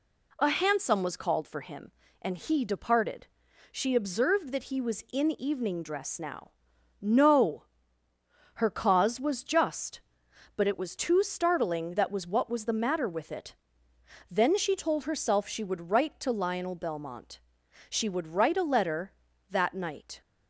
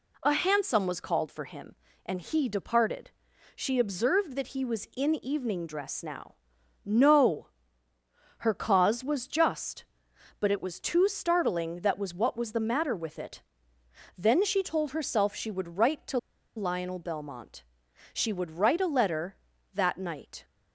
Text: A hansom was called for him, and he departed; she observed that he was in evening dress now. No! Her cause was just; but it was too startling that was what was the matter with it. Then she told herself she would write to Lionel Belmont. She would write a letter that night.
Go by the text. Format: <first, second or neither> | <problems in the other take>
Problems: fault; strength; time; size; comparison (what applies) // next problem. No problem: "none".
first | pauses between "to" and "Lionel"; at 16.1 s; 0.38 s long